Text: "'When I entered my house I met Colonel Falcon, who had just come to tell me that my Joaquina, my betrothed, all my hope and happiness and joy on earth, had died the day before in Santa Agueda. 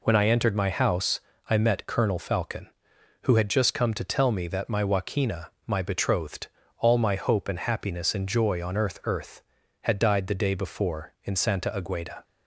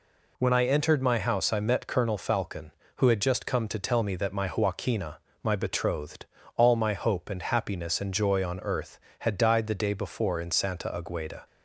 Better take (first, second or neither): second